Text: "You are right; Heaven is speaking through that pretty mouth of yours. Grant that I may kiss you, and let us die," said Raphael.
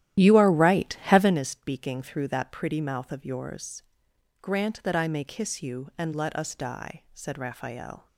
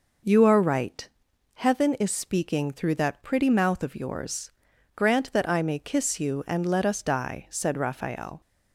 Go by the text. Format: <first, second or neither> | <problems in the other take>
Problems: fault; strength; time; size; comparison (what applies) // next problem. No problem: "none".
second | starts louder than the rest; strong; until 1.3 s; 12.5 dB